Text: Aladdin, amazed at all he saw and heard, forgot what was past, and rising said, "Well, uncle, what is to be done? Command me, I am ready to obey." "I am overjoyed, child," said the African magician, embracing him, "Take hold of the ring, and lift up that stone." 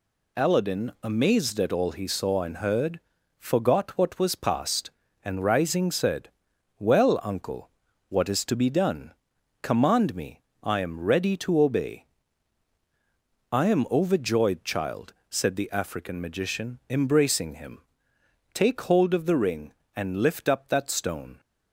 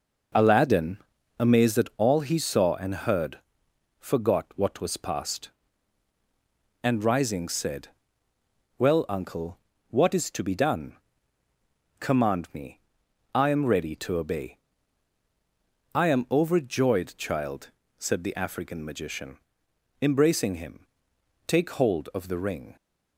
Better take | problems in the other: first | stops before "and lift up that stone"; at 22.7 s

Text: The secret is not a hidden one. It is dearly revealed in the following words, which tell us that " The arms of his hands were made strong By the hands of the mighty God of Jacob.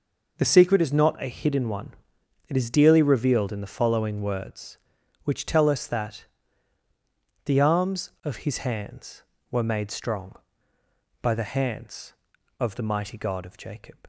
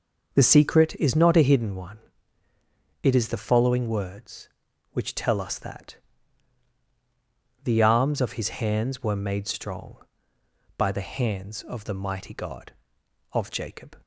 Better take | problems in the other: first | skips "dearly revealed in"; at 3.2 s

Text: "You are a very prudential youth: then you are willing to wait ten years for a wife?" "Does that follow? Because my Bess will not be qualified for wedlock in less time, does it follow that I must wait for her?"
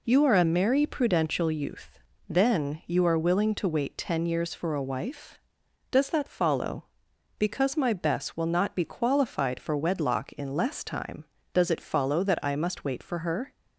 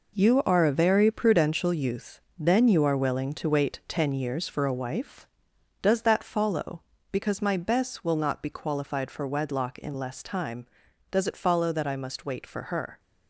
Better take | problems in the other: second | says "merry" for "very"; at 0.4 s

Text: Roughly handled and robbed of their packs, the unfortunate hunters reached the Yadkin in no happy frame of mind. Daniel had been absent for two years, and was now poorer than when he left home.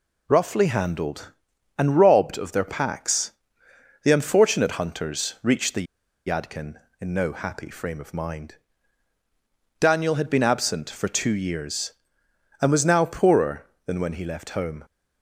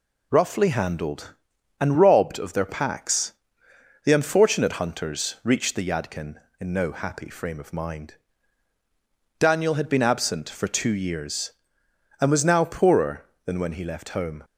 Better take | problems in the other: second | pauses between "the" and "Yadkin"; at 5.8 s; 0.40 s long

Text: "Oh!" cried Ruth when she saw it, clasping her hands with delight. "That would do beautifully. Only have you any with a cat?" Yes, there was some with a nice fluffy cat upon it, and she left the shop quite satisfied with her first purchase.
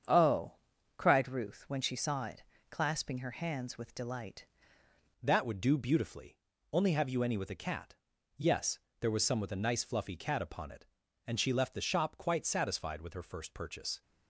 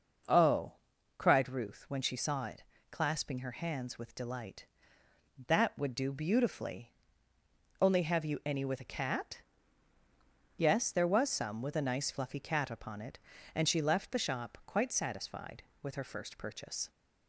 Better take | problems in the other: second | starts louder than the rest; strong; until 1.5 s; 7.5 dB // changes voice at "That"; from 5.2 s on; 8.8 s long

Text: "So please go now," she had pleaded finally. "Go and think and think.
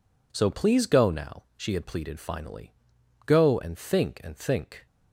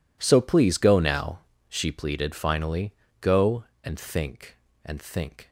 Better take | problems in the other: first | skips "had"; at 1.9 s

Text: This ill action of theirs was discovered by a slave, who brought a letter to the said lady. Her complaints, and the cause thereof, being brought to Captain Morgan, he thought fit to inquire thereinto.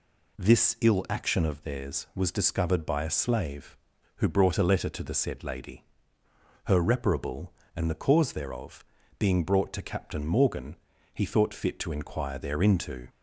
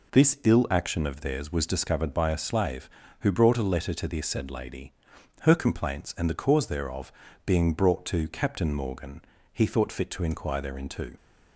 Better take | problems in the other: second | says "reparable" for "complaints"; at 6.8 s

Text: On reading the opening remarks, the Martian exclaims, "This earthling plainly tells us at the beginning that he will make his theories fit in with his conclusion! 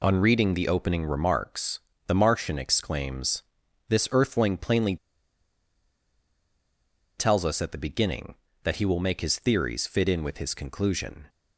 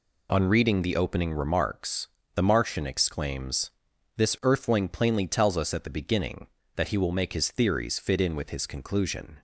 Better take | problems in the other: second | pauses between "plainly" and "tells"; strong; at 4.9 s; 2.2 s long

